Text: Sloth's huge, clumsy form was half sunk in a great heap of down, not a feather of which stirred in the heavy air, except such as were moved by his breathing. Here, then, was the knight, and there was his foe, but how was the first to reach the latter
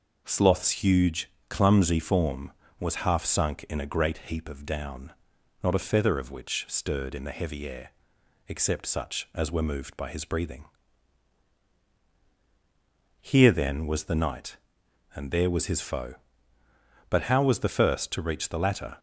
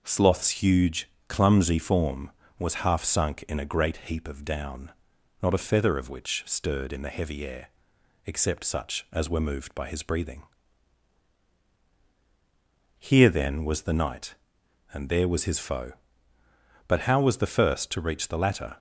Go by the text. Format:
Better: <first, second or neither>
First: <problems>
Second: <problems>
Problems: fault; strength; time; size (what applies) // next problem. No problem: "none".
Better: neither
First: none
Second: none